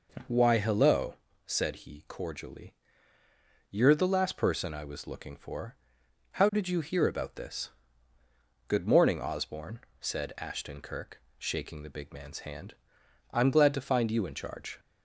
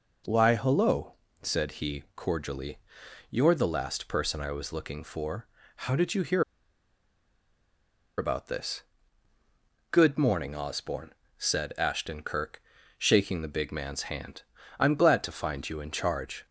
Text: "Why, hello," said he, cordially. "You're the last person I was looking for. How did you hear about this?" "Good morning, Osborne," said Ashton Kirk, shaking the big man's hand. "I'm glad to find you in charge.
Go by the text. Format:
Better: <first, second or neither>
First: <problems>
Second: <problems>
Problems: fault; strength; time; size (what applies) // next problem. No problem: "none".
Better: first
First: none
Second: pauses between "hear" and "about"; strong; at 6.4 s; 1.7 s long